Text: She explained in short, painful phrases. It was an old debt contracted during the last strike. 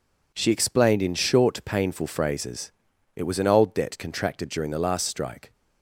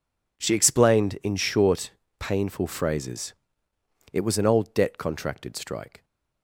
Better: first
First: none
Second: skips "during the last"; at 5.5 s

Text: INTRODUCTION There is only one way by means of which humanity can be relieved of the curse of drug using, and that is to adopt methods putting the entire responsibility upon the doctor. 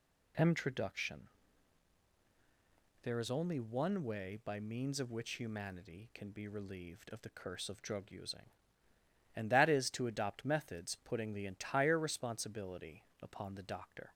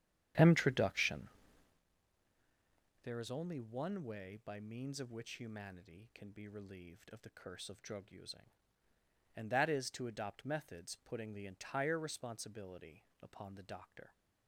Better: first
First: pauses between "INTRODUCTION" and "There"; strong; at 1.2 s; 1.7 s long // pauses between "responsibility" and "upon"; slight; at 13.0 s; 0.18 s long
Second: starts louder than the rest; strong; until 1.8 s; 10 dB // pauses between "INTRODUCTION" and "There"; strong; at 1.2 s; 1.7 s long // pauses between "responsibility" and "upon"; slight; at 13.0 s; 0.18 s long

